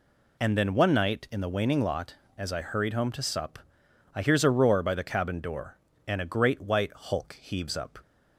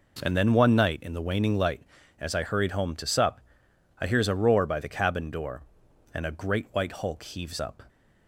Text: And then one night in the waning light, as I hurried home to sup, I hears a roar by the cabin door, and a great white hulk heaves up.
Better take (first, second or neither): second